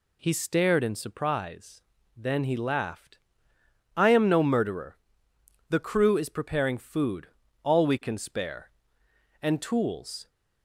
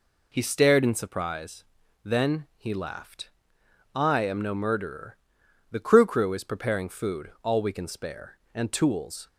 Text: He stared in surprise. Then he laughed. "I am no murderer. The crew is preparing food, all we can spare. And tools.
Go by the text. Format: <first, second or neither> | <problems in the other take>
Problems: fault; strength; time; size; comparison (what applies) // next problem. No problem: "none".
first | says "crew" twice; at 6.0 s